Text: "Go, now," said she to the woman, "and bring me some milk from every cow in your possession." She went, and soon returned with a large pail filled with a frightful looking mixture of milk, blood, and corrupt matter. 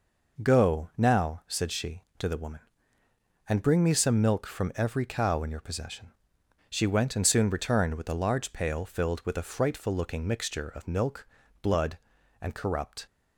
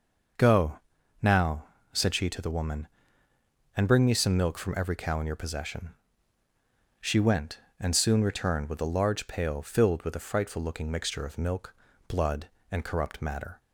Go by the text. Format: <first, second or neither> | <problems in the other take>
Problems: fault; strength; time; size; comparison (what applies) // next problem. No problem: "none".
second | stops before "matter"; at 13.0 s